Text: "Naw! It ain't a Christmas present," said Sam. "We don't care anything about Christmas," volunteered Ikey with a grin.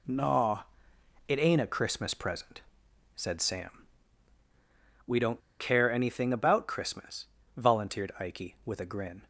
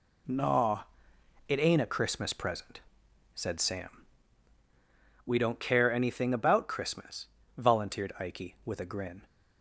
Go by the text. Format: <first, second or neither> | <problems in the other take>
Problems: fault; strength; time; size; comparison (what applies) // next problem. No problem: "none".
second | pauses between "don't" and "care"; slight; at 5.4 s; 0.18 s long